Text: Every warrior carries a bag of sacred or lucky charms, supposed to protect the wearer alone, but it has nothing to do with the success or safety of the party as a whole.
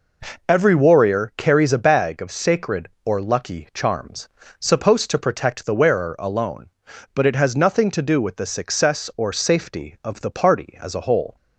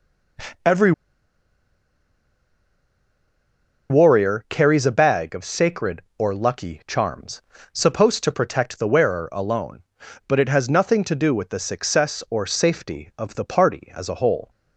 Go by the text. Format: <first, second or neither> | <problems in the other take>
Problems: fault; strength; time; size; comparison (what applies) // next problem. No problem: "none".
first | pauses between "Every" and "warrior"; strong; at 0.9 s; 2.9 s long